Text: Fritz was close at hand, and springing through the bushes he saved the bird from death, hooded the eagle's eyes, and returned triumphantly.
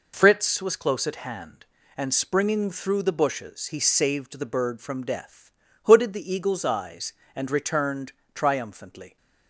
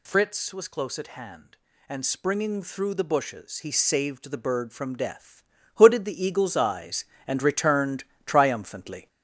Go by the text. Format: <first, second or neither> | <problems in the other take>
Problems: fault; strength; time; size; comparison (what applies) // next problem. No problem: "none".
first | gets louder; noticeable; throughout; 5 dB // pauses between "returned" and "triumphantly"; slight; at 8.0 s; 0.20 s long; slight in the first